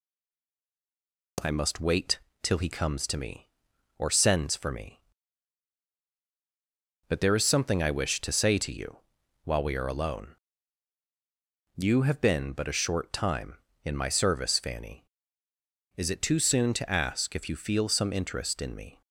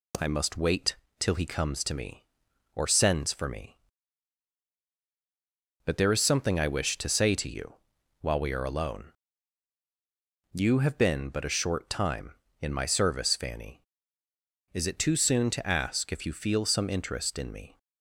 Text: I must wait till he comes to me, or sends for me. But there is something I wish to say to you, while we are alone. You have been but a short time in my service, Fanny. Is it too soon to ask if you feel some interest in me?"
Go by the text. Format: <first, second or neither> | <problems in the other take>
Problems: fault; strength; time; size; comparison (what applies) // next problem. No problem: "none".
second | stays silent before the first word; noticeable; until 1.3 s; 1.3 s long // pauses between "wait" and "till"; slight; at 2.1 s; 0.24 s long; slight in the second